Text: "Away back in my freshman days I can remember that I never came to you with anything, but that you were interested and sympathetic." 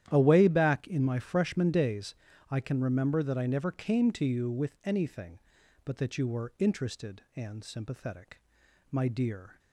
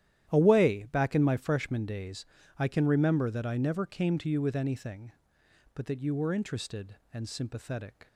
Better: second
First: starts louder than the rest; strong; until 1.0 s; 11 dB // pauses between "days" and "I"; slight; at 2.1 s; 0.34 s long // goes on to say "My dear"; noticeable; from 8.9 s on; 0.66 s long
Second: starts louder than the rest; strong; until 1.3 s; 11 dB // pauses between "days" and "I"; slight; at 2.2 s; 0.32 s long

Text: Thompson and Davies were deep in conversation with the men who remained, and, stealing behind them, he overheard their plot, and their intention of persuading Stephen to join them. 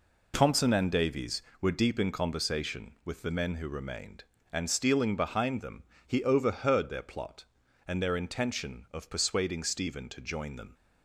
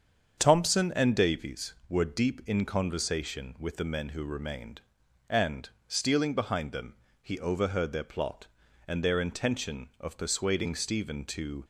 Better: first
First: none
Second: starts louder than the rest; strong; until 1.3 s; 7.5 dB // stops before "join them"; at 11.6 s

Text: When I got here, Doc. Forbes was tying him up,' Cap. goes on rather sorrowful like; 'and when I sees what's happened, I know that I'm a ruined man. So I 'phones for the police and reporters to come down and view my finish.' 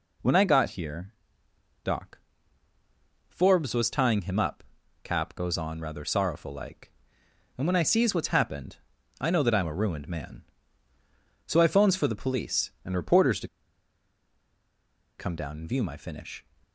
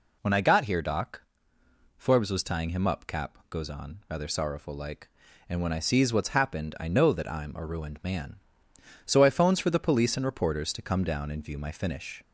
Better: second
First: pauses between "to" and "come"; strong; at 13.4 s; 1.7 s long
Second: none

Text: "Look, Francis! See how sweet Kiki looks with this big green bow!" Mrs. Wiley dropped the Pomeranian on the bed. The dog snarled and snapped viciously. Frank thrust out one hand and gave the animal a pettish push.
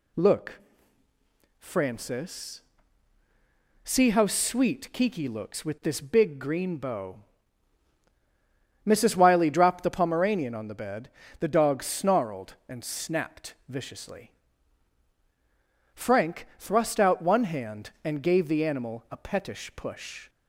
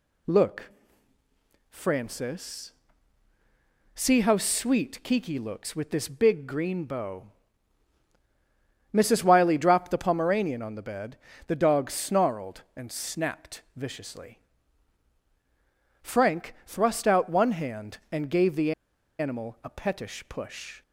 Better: first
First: pauses between "snapped" and "viciously"; slight; at 13.5 s; 0.16 s long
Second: pauses between "snapped" and "viciously"; slight; at 13.6 s; 0.16 s long // pauses between "the" and "animal"; noticeable; at 18.7 s; 0.46 s long

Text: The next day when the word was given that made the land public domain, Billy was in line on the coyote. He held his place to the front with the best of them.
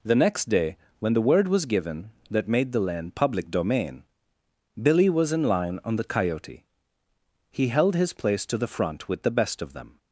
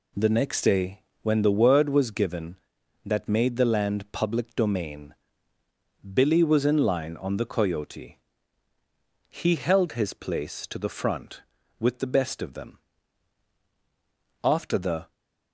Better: first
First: pauses between "day" and "when"; slight; at 0.7 s; 0.20 s long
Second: pauses between "day" and "when"; slight; at 1.0 s; 0.22 s long // goes on to say "After the"; noticeable; from 14.4 s on; 0.70 s long

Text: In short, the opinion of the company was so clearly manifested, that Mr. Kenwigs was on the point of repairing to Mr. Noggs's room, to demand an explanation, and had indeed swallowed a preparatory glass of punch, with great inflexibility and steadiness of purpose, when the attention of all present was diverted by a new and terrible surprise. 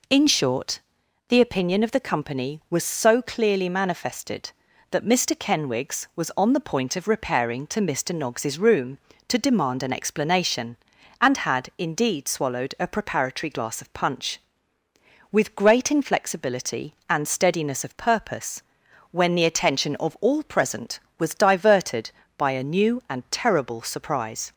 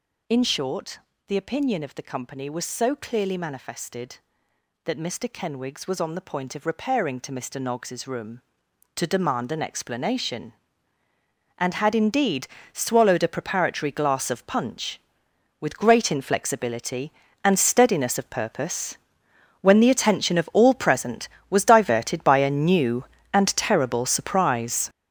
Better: first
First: none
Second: gets louder; strong; throughout; 10 dB // pauses between "indeed" and "swallowed"; slight; at 12.4 s; 0.26 s long

